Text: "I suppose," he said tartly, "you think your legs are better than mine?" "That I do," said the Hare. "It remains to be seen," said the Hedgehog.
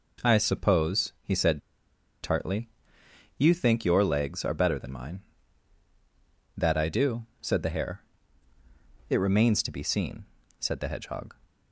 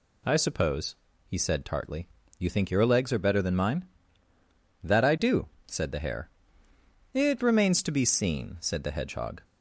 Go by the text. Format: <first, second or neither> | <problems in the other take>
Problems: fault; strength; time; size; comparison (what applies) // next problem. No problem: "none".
second | pauses between "said" and "tartly"; noticeable; at 1.6 s; 0.61 s long